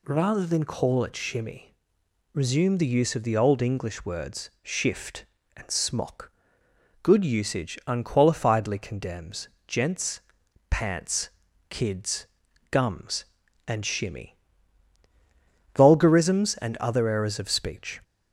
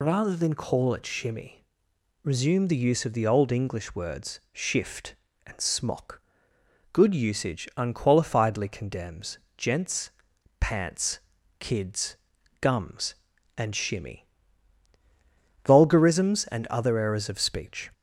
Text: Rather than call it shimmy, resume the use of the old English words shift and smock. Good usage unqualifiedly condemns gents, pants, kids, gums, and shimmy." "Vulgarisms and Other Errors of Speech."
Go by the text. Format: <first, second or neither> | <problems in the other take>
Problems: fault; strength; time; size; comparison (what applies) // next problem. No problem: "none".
first | loses the start of "Rather"; at 0.0 s; 55 ms // pauses between "condemns" and "gents"; slight; at 9.3 s; 0.18 s long; slight in the first